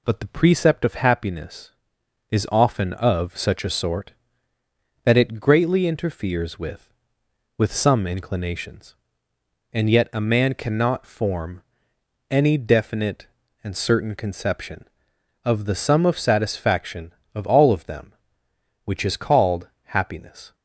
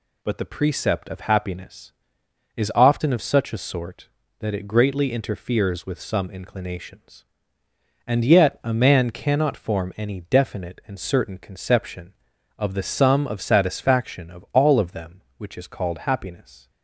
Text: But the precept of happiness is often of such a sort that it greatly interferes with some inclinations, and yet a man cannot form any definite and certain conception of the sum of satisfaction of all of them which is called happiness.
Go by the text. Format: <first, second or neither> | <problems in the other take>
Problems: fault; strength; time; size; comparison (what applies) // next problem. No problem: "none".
second | says "with" twice; at 7.5 s // pauses between "form" and "any"; noticeable; at 11.6 s; 0.66 s long // pauses between "called" and "happiness"; slight; at 19.6 s; 0.16 s long